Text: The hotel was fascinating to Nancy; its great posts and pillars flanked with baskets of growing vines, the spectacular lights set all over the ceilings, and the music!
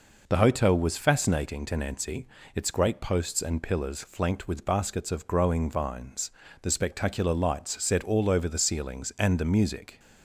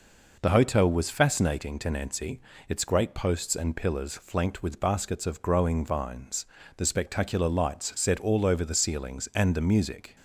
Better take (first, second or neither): neither